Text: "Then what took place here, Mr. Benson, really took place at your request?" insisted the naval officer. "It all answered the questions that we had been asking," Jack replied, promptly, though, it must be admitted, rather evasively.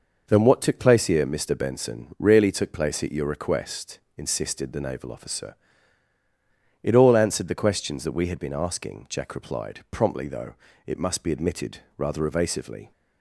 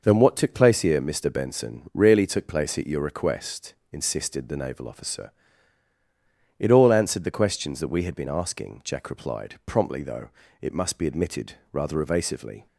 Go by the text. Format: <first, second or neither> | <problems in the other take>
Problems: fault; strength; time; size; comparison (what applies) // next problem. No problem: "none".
neither | none